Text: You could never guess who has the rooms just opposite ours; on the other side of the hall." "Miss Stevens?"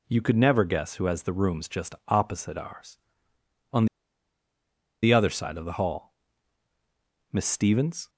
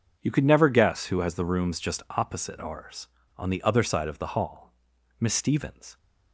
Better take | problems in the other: second | pauses between "on" and "the"; at 3.8 s; 1.1 s long

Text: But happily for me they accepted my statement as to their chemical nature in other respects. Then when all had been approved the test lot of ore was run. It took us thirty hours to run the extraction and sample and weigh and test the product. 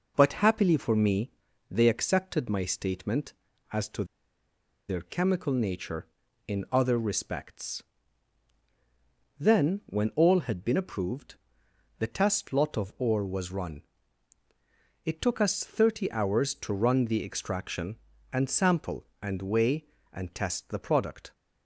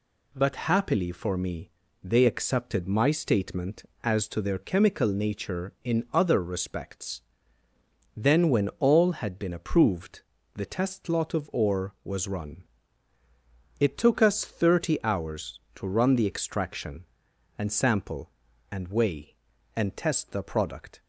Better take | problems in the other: second | pauses between "me" and "they"; at 1.3 s; 0.40 s long; slight in the second // pauses between "to" and "their"; noticeable; at 4.0 s; 0.84 s long // pauses between "approved" and "the"; noticeable; at 11.3 s; 0.62 s long; slight in the second

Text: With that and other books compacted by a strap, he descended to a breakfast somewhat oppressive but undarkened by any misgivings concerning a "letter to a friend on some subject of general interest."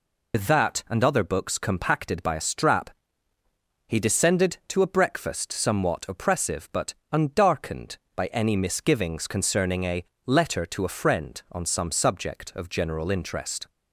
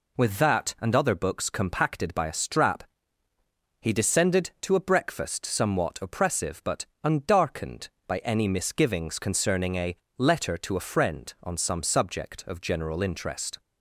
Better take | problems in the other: second | loses the start of "With"; at 0.3 s; 80 ms // pauses between "but" and "undarkened"; slight; at 6.9 s; 0.18 s long; slight in the second // pauses between "a" and "letter"; slight; at 10.0 s; 0.22 s long; slight in the second

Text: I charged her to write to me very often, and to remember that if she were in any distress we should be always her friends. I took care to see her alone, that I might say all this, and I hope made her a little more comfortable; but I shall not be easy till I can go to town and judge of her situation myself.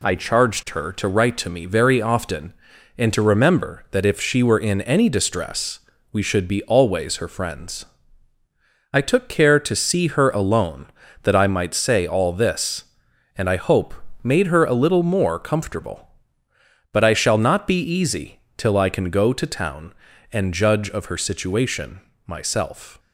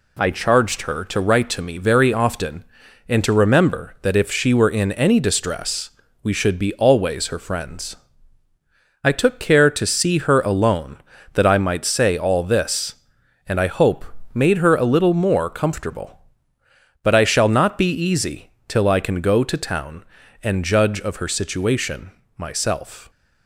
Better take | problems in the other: neither | pauses between "distress" and "we"; slight; the same in both // pauses between "hope" and "made"; slight; the same in both // pauses between "easy" and "till"; slight; the same in both // pauses between "situation" and "myself"; slight; the same in both

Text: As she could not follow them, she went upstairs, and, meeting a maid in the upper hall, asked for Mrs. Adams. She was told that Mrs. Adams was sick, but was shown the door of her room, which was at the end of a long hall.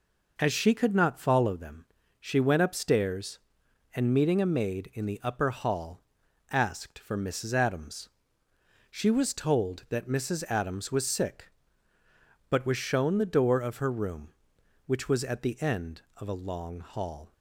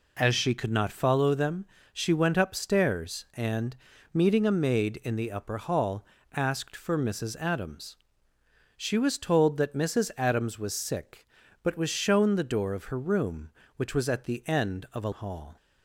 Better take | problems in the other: first | skips "long"; at 15.1 s

